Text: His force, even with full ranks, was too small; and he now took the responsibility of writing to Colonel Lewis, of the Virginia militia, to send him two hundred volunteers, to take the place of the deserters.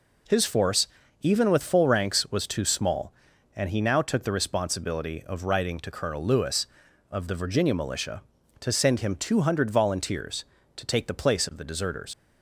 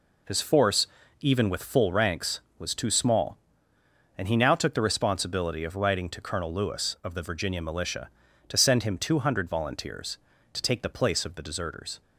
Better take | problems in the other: second | leaves "deserters" unfinished; at 12.1 s; 65 ms

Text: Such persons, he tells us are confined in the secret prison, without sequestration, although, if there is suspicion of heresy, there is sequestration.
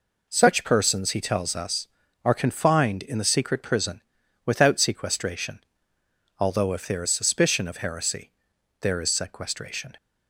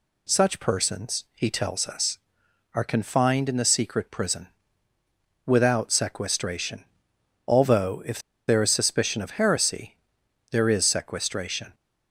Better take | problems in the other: first | pauses between "if" and "there"; slight; at 8.1 s; 0.28 s long

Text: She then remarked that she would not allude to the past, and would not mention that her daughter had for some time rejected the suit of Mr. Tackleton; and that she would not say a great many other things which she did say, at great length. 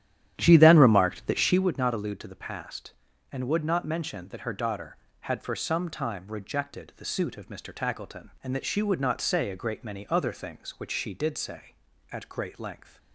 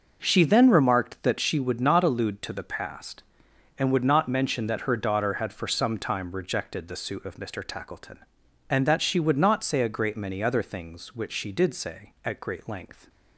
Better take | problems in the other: second | starts louder than the rest; strong; until 1.7 s; 11 dB

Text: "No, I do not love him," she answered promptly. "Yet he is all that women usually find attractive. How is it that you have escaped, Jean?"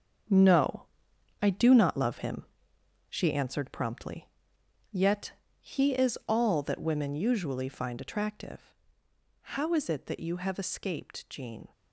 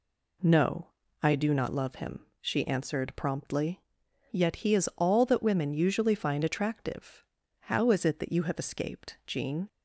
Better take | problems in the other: second | gets quieter; strong; throughout; 10 dB // pauses between "Yet" and "he"; slight; at 5.3 s; 0.30 s long

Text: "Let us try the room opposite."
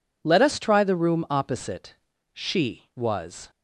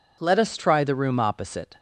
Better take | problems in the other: second | goes on to say "She was"; noticeable; from 2.3 s on; 1.1 s long

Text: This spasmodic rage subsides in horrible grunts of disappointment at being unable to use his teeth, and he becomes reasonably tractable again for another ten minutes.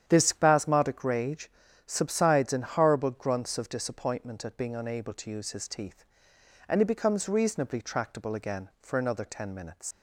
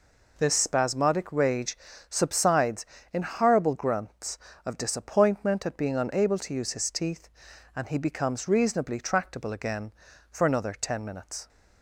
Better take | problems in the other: second | starts louder than the rest; strong; until 1.0 s; 9.5 dB // pauses between "rage" and "subsides"; slight; at 1.5 s; 0.34 s long; slight in the second // leaves "minutes" unfinished; at 9.9 s; 75 ms

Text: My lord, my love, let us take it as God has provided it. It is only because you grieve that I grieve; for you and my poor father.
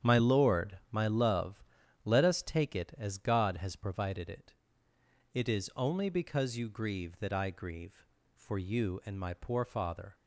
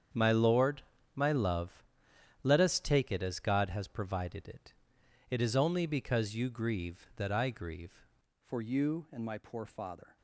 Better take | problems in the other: first | starts louder than the rest; strong; until 1.4 s; 8 dB; strong in the first // changes voice at "for"; from 8.4 s on; 1.7 s long

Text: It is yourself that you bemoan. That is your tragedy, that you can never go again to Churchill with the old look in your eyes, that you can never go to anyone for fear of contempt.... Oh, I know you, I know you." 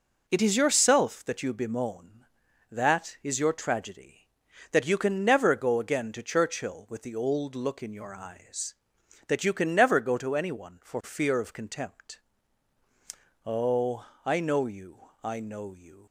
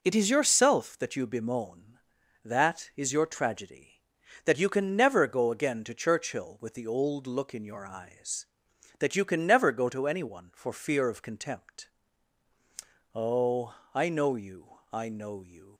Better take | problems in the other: neither | none

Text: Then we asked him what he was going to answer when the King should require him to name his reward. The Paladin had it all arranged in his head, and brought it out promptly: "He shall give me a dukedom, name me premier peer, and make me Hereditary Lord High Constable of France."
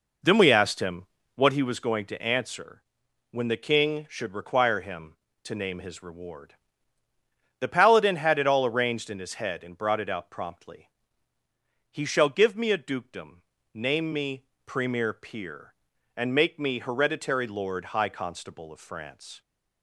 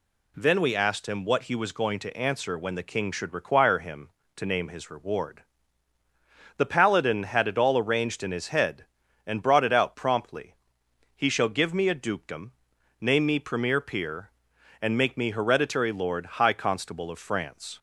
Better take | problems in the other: second | starts louder than the rest; noticeable; until 1.8 s; 4.5 dB // pauses between "him" and "what"; slight; at 1.0 s; 0.28 s long // pauses between "answer" and "when"; noticeable; at 2.8 s; 0.48 s long // pauses between "me" and "premier"; slight; at 14.4 s; 0.22 s long

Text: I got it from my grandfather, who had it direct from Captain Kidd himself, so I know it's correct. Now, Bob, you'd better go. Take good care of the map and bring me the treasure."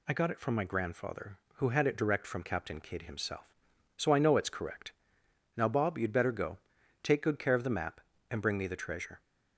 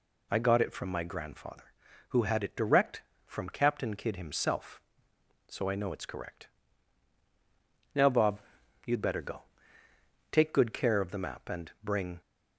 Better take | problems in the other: first | stops before "me the treasure"; at 12.2 s

